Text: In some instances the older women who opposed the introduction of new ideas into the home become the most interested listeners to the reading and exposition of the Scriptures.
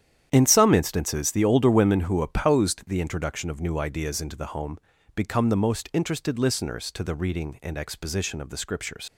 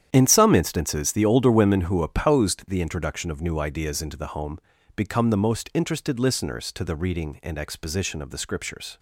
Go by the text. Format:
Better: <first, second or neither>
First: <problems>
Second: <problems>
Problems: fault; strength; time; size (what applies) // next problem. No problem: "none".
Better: second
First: starts louder than the rest; strong; until 1.3 s; 10 dB // pauses between "home" and "become"; at 4.7 s; 0.38 s long // leaves "Scriptures" unfinished; at 9.0 s; 100 ms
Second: starts louder than the rest; strong; until 1.1 s; 10 dB // pauses between "home" and "become"; at 4.5 s; 0.38 s long